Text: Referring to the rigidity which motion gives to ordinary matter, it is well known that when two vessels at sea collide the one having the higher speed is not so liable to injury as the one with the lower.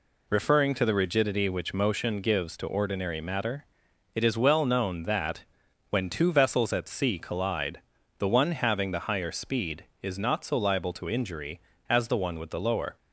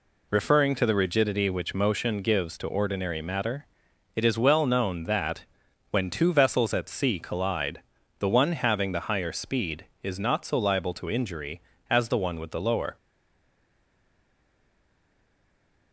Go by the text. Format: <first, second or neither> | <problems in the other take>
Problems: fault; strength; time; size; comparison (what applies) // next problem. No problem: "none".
first | pauses between "that" and "when"; noticeable; at 5.4 s; 0.46 s long; noticeable in the first // pauses between "collide" and "the"; at 7.8 s; 0.40 s long; also in the first // stays silent after the last word; strong; from 12.9 s on; 3.0 s long